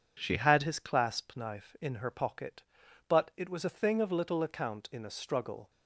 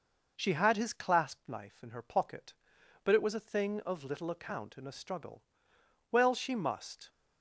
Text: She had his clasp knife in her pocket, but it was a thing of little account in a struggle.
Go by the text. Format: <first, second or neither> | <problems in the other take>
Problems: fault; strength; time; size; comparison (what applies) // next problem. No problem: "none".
first | goes on to say "Well she must"; noticeable; from 6.1 s on; 0.98 s long